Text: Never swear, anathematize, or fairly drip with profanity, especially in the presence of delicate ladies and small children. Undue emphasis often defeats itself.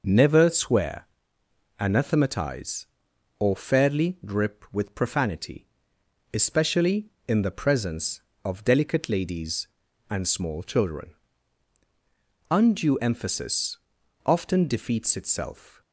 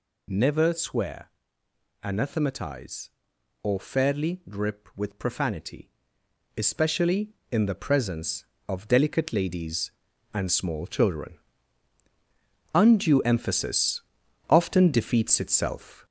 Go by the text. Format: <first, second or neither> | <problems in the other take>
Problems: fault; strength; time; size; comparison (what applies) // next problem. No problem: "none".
first | gets louder; noticeable; throughout; 5 dB // pauses between "emphasis" and "often"; noticeable; at 14.0 s; 0.48 s long; noticeable in the first